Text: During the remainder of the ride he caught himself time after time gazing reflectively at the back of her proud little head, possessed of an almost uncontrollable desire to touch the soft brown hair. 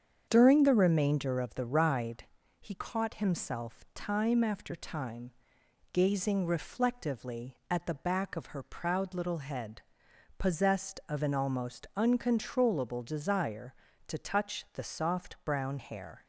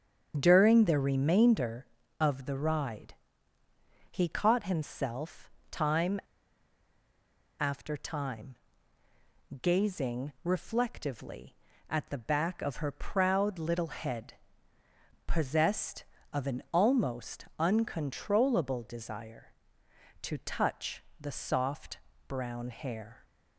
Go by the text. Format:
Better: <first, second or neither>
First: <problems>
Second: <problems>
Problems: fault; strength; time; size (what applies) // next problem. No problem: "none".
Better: first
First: starts louder than the rest; strong; until 1.3 s; 7.5 dB // pauses between "ride" and "he"; slight; at 2.2 s; 0.34 s long // pauses between "time" and "gazing"; noticeable; at 5.2 s; 0.62 s long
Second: starts louder than the rest; strong; until 1.3 s; 7.5 dB // pauses between "ride" and "he"; noticeable; at 3.1 s; 0.98 s long // pauses between "himself" and "time"; slight; at 5.4 s; 0.22 s long // pauses between "time" and "after"; strong; at 6.1 s; 1.4 s long // pauses between "time" and "gazing"; at 8.5 s; 1.0 s long // pauses between "touch" and "the"; slight; at 21.0 s; 0.18 s long // pauses between "soft" and "brown"; slight; at 21.9 s; 0.30 s long